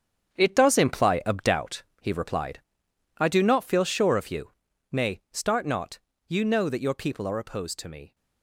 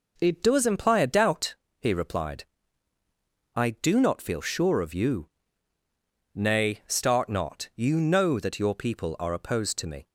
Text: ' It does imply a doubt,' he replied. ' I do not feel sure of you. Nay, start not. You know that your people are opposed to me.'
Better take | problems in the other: second | gets quieter; noticeable; throughout; 6 dB

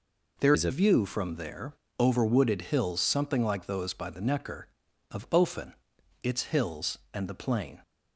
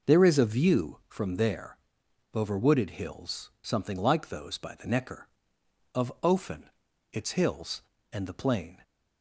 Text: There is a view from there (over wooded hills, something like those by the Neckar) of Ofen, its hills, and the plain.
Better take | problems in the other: second | changes voice from "is" to "a"; from 0.5 to 0.7 s; 0.2 s long

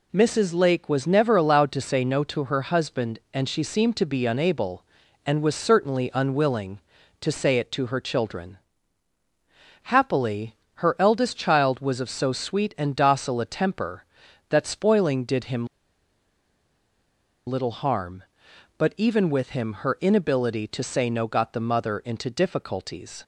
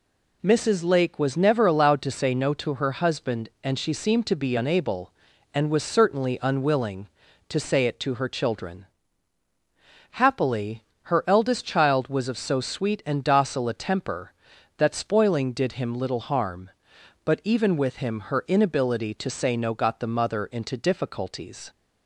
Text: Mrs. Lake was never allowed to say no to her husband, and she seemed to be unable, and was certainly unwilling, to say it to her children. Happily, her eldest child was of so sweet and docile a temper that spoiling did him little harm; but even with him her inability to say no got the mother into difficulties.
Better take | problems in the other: second | pauses between "him" and "little"; strong; at 15.6 s; 1.8 s long

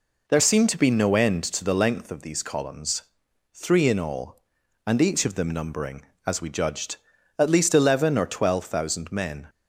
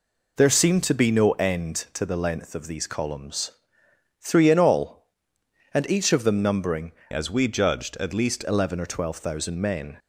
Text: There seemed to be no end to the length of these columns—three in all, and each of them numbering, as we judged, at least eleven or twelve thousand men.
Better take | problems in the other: first | changes voice from "as" to "least"; from 7.1 to 8.4 s; 1.3 s long

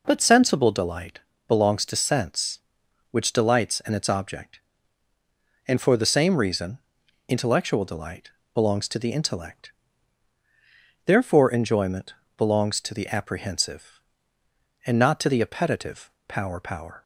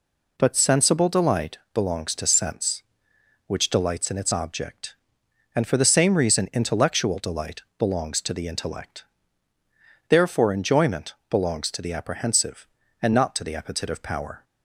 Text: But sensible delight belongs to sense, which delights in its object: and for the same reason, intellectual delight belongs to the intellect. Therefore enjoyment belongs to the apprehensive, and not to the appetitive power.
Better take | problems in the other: second | pauses between "delight" and "belongs"; slight; at 1.1 s; 0.30 s long; slight in the second // pauses between "delight" and "belongs"; slight; at 8.2 s; 0.24 s long; slight in the second // pauses between "enjoyment" and "belongs"; slight; at 12.1 s; 0.24 s long; slight in the second // pauses between "appetitive" and "power"; slight; at 16.1 s; 0.18 s long // says "power" twice; at 16.6 s

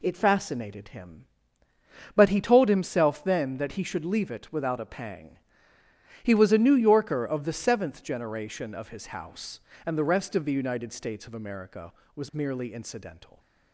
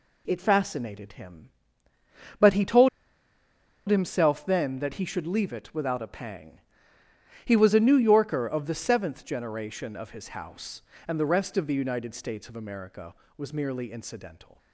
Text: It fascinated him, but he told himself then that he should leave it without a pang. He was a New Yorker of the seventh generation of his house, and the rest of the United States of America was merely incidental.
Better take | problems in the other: first | pauses between "told" and "himself"; at 2.8 s; 1.0 s long

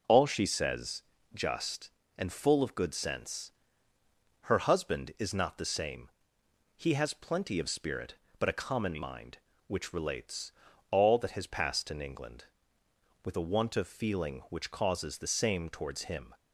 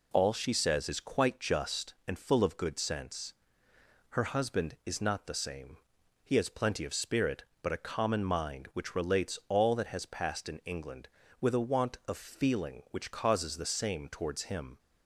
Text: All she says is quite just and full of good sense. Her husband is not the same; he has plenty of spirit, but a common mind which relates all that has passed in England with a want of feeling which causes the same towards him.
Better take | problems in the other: second | skips "is quite"; at 1.1 s // pauses between "relates" and "all"; at 10.5 s; 0.40 s long

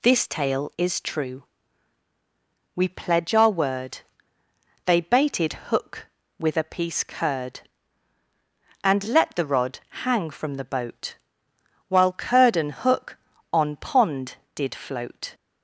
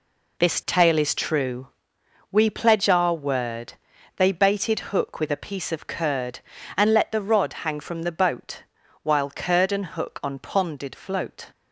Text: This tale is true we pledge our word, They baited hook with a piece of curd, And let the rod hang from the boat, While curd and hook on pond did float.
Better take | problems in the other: second | pauses between "true" and "we"; strong; at 1.4 s; 1.3 s long; noticeable in the second // skips "of"; at 7.0 s // pauses between "rod" and "hang"; slight; at 9.8 s; 0.24 s long

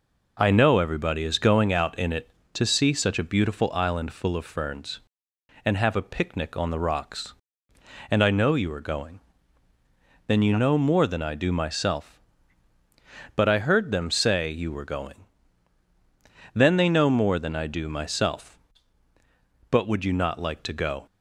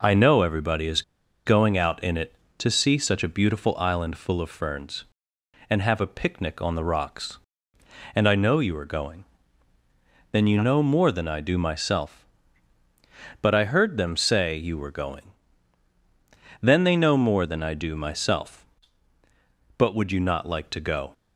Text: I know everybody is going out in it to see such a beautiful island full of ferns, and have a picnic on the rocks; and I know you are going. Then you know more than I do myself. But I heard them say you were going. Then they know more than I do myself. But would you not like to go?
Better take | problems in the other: first | pauses between "is" and "going"; at 1.0 s; 0.42 s long

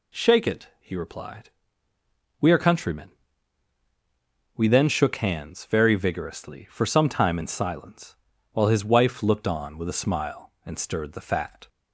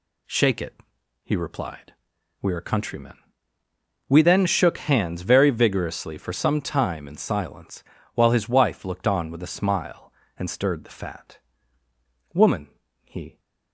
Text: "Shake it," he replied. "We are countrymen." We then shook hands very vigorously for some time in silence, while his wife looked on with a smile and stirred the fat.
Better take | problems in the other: first | goes on to say "Woman he"; noticeable; from 12.3 s on; 1.0 s long

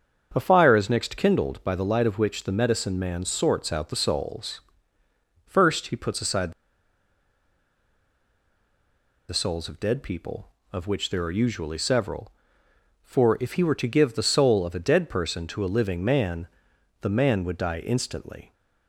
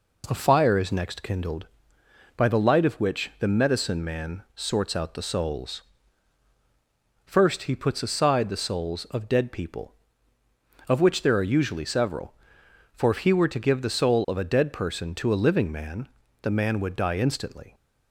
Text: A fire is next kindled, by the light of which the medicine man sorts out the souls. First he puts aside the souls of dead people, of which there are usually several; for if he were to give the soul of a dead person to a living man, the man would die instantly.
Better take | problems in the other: second | starts louder than the rest; strong; until 1.3 s; 7 dB // pauses between "aside" and "the"; strong; at 6.5 s; 2.7 s long

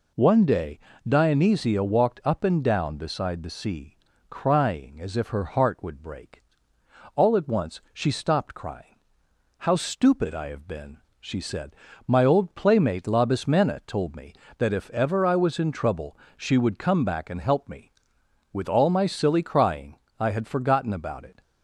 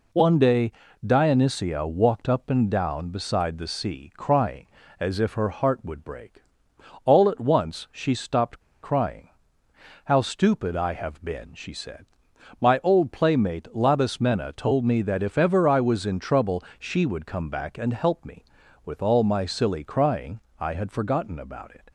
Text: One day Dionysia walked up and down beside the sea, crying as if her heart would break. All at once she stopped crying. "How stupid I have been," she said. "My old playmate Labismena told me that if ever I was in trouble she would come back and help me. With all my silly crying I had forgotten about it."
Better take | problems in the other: first | pauses between "day" and "Dionysia"; slight; at 0.7 s; 0.34 s long; slight in the first // pauses between "stopped" and "crying"; slight; at 8.5 s; 0.23 s long // pauses between "trouble" and "she"; slight; at 16.6 s; 0.16 s long; slight in the first // pauses between "crying" and "I"; slight; at 20.4 s; 0.18 s long; slight in the first

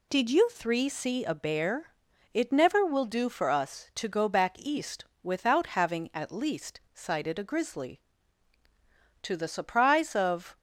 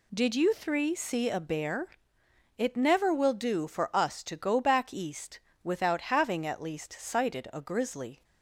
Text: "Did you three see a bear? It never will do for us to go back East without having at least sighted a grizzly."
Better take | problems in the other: second | pauses between "East" and "without"; slight; at 5.0 s; 0.18 s long; slight in the second // goes on to say "To the surprise of"; from 9.2 s on; 1.3 s long

